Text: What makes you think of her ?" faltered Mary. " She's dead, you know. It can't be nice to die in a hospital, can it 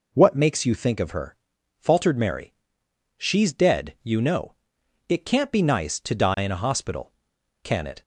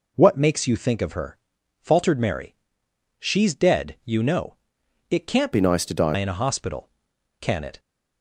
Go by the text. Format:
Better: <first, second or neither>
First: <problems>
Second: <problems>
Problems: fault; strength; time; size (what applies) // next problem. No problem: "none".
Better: first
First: none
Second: changes voice from "be" to "die"; from 5.5 to 6.1 s; 0.6 s long